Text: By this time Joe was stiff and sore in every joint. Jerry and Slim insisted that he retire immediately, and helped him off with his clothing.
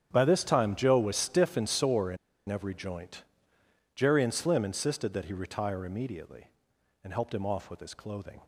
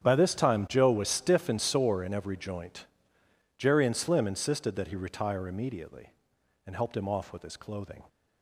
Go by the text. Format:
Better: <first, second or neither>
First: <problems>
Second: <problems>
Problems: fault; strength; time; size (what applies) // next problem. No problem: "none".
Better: second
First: starts louder than the rest; strong; until 1.1 s; 9 dB // pauses between "in" and "every"; slight; at 2.1 s; 0.32 s long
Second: starts louder than the rest; strong; until 1.0 s; 8.5 dB